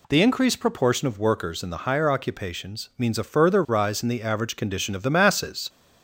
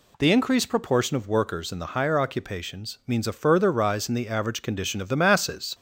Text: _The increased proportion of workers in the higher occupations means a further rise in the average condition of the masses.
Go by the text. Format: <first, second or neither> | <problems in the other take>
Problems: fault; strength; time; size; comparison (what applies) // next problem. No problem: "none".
neither | none